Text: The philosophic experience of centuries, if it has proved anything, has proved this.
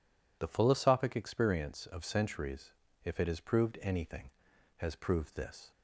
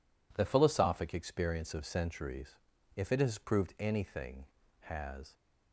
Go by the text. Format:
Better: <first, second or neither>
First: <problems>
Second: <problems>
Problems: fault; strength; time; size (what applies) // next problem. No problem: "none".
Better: first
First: none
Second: stops before "proved this"; at 5.3 s